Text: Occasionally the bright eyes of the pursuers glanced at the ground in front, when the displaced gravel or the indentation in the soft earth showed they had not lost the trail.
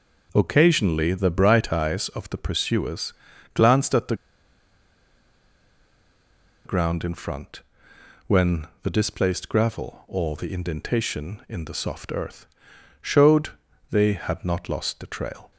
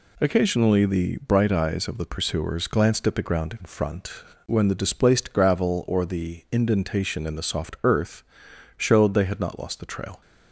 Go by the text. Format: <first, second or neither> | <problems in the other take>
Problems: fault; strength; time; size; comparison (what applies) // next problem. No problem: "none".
second | pauses between "pursuers" and "glanced"; at 3.1 s; 0.42 s long // pauses between "the" and "ground"; strong; at 4.1 s; 2.5 s long // pauses between "earth" and "showed"; noticeable; at 12.4 s; 0.56 s long; noticeable in the second // pauses between "showed" and "they"; at 13.4 s; 0.42 s long